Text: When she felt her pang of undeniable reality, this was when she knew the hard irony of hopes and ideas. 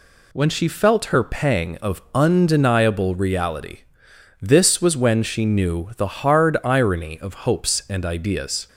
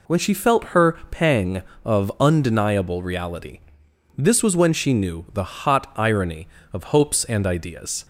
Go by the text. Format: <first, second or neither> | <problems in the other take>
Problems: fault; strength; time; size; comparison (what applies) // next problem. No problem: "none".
first | pauses between "her" and "pang"; slight; at 0.9 s; 0.16 s long // says "hot" for "hard"; at 5.4 s